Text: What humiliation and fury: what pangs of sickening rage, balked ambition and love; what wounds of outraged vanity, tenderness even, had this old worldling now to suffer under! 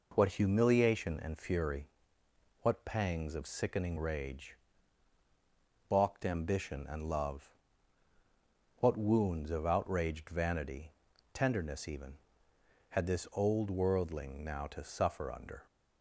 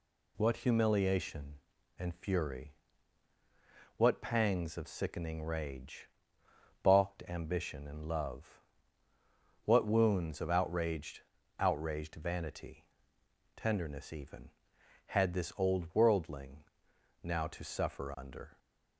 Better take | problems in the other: first | says "outraged" twice; at 11.5 s // pauses between "worldling" and "now"; noticeable; at 16.6 s; 0.60 s long

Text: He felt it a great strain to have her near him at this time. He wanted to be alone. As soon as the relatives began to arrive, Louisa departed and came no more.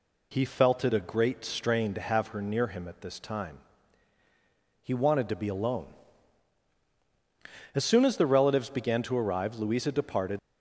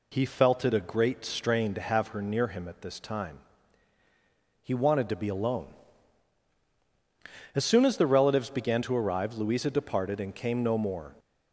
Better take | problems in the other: second | stops before "and came no more"; at 10.3 s

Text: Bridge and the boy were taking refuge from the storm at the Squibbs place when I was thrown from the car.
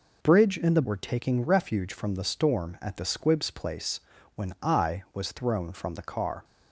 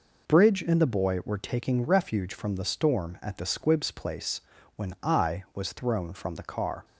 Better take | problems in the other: second | skips "boy"; at 0.8 s // pauses between "place" and "when"; slight; at 3.9 s; 0.36 s long; slight in the second

